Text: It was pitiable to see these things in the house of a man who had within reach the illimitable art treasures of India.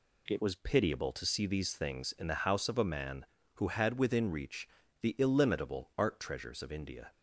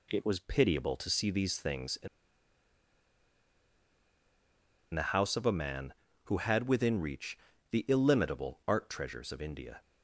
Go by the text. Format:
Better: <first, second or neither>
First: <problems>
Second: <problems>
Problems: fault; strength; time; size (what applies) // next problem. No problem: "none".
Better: first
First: pauses between "reach" and "the"; slight; at 4.6 s; 0.34 s long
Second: pauses between "in" and "the"; strong; at 2.0 s; 2.8 s long // pauses between "reach" and "the"; slight; at 7.3 s; 0.34 s long